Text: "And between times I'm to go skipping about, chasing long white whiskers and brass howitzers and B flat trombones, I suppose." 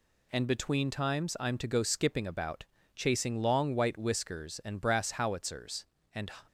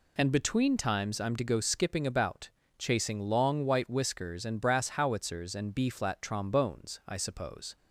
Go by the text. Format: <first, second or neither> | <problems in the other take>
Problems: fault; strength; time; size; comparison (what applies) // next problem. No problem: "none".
second | stops before "B flat trombones I suppose"; at 6.4 s